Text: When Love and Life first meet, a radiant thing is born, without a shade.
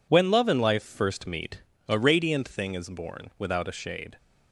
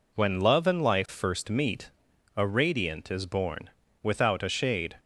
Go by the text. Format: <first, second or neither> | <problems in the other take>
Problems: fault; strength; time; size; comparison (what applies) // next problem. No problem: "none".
first | skips "thing"; at 3.1 s